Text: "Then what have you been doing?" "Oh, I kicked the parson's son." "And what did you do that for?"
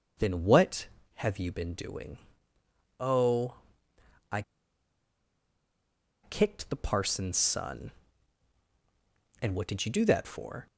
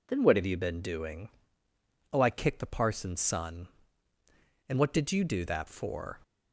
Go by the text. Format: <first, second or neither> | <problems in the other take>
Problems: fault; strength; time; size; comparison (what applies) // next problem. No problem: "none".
second | pauses between "I" and "kicked"; strong; at 4.4 s; 1.8 s long